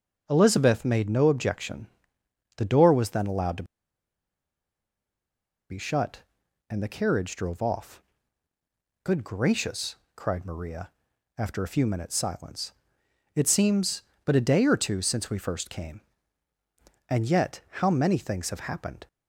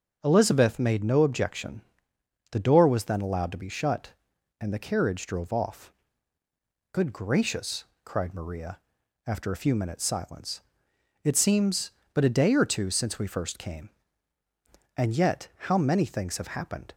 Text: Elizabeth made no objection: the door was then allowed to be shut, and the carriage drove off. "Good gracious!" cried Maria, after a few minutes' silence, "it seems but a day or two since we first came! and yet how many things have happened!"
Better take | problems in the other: second | starts louder than the rest; until 1.2 s; 6.5 dB; also in the second // pauses between "to" and "be"; strong; at 3.6 s; 2.0 s long // pauses between "yet" and "how"; slight; at 17.6 s; 0.20 s long; slight in the second

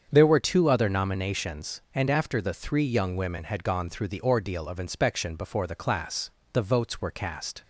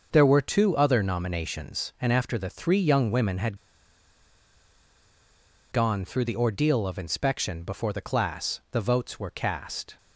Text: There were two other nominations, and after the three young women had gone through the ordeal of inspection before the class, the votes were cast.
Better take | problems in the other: first | starts louder than the rest; until 1.1 s; 6.5 dB; strong in the first // pauses between "had" and "gone"; strong; at 3.5 s; 2.1 s long

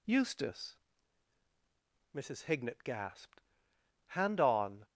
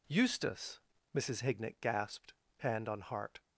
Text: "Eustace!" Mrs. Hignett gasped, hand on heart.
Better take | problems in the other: second | stops before "heart"; at 4.8 s

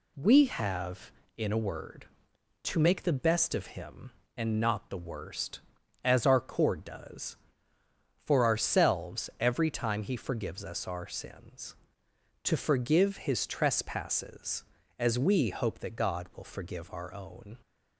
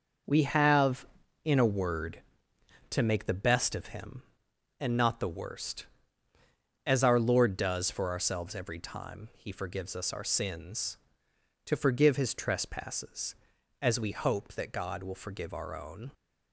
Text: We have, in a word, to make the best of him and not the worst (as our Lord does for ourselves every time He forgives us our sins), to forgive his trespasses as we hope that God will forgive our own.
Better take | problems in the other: second | says "Cord" for "Lord"; at 6.3 s

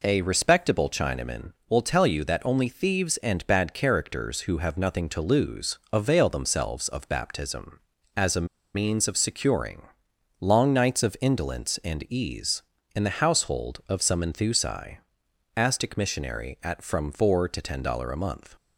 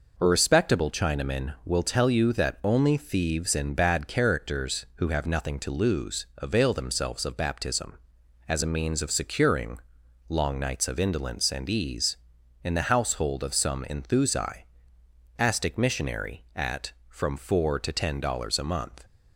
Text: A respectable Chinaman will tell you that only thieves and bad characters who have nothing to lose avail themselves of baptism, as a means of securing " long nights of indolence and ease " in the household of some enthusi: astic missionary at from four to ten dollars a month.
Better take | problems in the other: second | pauses between "a" and "means"; slight; at 8.4 s; 0.29 s long

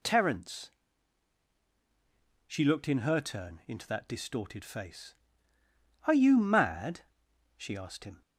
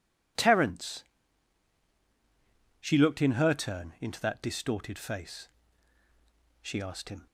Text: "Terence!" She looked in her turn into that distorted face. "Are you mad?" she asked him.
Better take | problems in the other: first | skips "Are you mad"; at 6.0 s

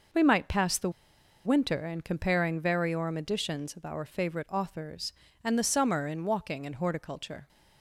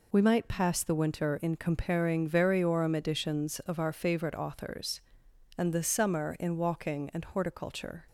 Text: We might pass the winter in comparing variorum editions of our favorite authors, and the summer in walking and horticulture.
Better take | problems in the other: second | pauses between "the" and "winter"; noticeable; at 0.8 s; 0.55 s long

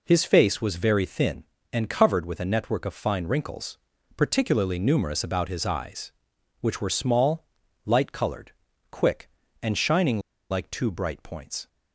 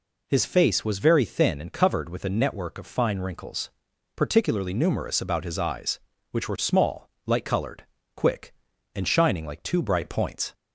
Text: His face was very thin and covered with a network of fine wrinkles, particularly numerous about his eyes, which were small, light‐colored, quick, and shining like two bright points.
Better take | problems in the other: second | pauses between "shining" and "like"; slight; at 10.1 s; 0.32 s long

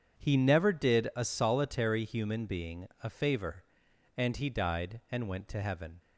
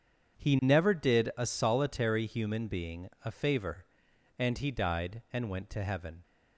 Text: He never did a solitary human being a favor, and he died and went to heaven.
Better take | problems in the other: neither | starts louder than the rest; strong; the same in both

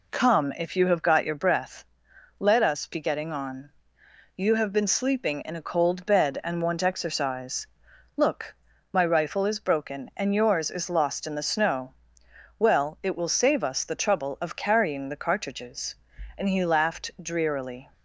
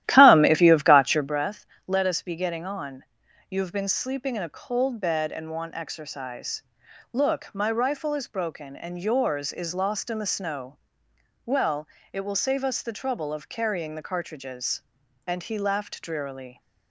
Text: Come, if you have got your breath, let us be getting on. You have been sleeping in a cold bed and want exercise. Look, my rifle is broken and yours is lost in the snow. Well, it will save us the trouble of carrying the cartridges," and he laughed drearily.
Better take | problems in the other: first | starts louder than the rest; strong; until 1.3 s; 13 dB

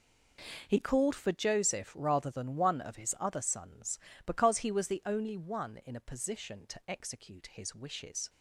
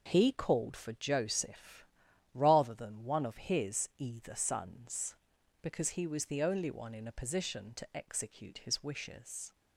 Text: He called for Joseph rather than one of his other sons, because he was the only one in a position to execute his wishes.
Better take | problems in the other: first | pauses between "Joseph" and "rather"; noticeable; at 1.8 s; 0.48 s long // says "either" for "other"; at 3.9 s

